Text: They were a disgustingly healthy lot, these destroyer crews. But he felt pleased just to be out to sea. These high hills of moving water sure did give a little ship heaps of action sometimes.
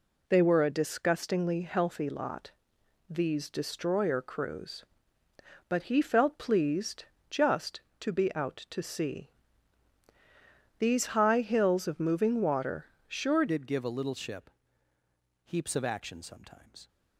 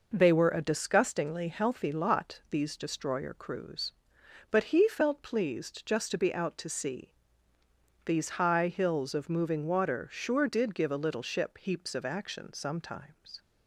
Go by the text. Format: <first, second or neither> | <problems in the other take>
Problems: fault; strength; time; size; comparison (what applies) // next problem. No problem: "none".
second | pauses between "pleased" and "just"; slight; at 7.0 s; 0.24 s long // pauses between "water" and "sure"; slight; at 12.8 s; 0.22 s long // changes voice at "did"; from 13.4 s on; 3.4 s long // pauses between "ship" and "heaps"; noticeable; at 14.5 s; 0.94 s long